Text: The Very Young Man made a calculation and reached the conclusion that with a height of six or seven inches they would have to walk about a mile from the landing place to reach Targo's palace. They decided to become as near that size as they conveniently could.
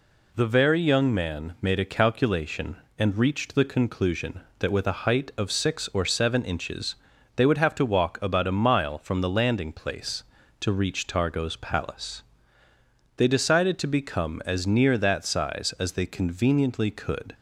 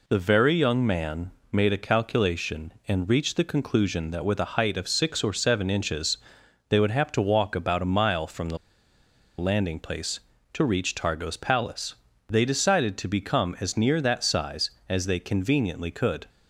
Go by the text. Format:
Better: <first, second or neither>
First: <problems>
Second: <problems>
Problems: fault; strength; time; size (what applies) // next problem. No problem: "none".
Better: first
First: pauses between "inches" and "they"; at 6.9 s; 0.40 s long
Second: pauses between "Man" and "made"; slight; at 1.3 s; 0.18 s long // pauses between "inches" and "they"; noticeable; at 6.1 s; 0.50 s long // pauses between "the" and "landing"; noticeable; at 8.5 s; 0.81 s long